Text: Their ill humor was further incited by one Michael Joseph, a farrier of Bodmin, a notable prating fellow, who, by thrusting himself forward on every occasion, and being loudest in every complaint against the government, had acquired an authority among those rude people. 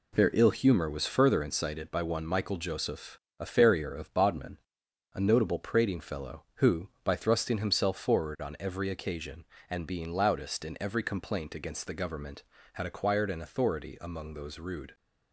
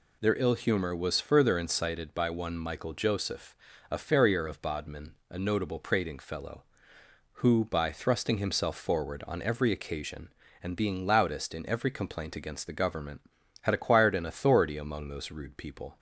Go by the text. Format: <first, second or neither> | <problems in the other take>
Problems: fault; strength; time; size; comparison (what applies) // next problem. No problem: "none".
second | stops before "people"; at 14.9 s